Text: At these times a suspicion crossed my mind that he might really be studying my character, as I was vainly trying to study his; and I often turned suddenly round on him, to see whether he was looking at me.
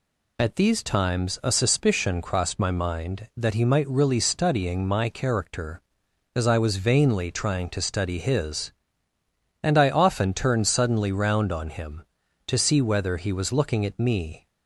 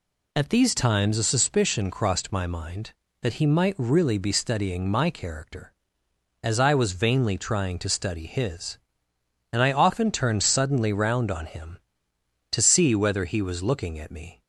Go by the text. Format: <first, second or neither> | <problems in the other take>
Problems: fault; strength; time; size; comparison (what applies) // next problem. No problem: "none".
second | skips "be"; at 4.1 s